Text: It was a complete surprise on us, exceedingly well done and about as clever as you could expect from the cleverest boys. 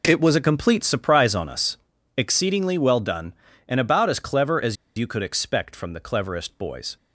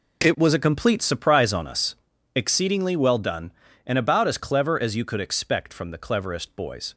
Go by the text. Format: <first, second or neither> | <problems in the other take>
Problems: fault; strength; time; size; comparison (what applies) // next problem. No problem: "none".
second | pauses between "as" and "you"; slight; at 4.7 s; 0.22 s long